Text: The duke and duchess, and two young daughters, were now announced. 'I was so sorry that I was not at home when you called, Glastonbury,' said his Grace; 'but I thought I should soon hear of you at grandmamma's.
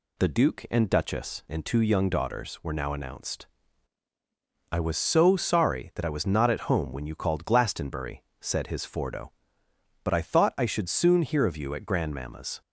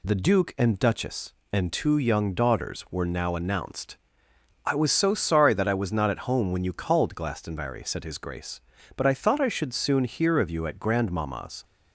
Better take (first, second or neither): second